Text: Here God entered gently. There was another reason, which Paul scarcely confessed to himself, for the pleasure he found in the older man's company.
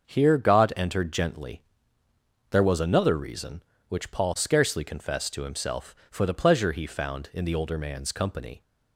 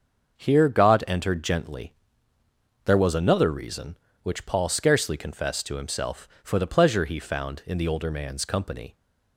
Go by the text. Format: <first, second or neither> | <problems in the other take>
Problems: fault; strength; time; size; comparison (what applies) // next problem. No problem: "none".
neither | starts louder than the rest; the same in both